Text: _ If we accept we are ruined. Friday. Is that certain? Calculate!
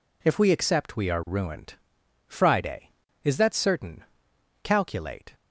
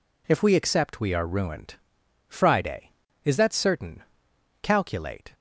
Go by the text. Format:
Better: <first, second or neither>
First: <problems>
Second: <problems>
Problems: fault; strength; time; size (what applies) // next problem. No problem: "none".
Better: neither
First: none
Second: none